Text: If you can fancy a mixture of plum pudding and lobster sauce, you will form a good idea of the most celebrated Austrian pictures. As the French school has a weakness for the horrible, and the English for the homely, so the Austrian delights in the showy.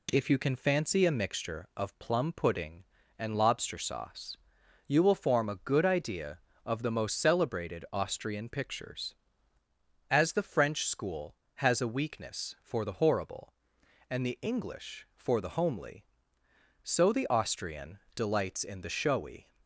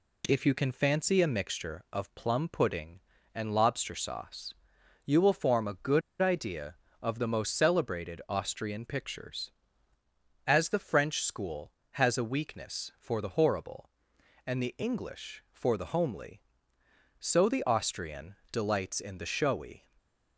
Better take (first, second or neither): first